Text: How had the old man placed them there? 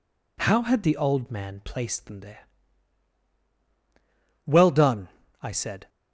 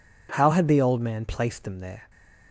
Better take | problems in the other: second | goes on to say "Well done I said"; from 4.4 s on; 1.4 s long

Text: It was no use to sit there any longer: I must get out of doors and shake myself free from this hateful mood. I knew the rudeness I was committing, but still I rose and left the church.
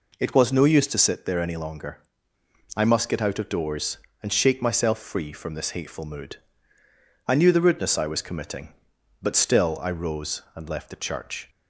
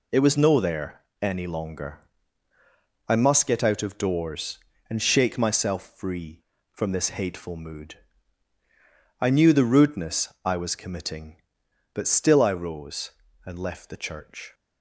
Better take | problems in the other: first | skips "use to sit"; at 0.5 s // pauses between "there" and "any"; slight; at 1.0 s; 0.18 s long

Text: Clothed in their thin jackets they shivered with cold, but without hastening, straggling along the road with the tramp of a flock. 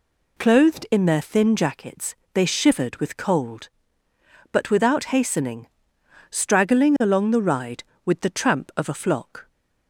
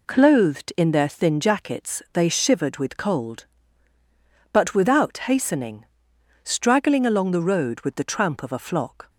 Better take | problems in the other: second | pauses between "jackets" and "they"; slight; at 2.1 s; 0.20 s long // says "ride" for "road"; at 7.4 s

